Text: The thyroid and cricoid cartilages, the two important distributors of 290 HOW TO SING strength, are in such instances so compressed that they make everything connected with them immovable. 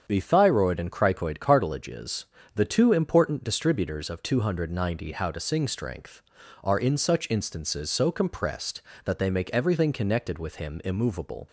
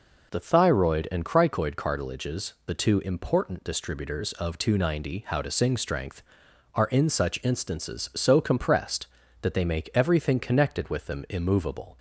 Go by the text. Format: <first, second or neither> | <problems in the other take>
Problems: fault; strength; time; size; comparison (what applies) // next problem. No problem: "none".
second | starts louder than the rest; strong; until 1.0 s; 7.5 dB // says "him" for "them"; at 10.5 s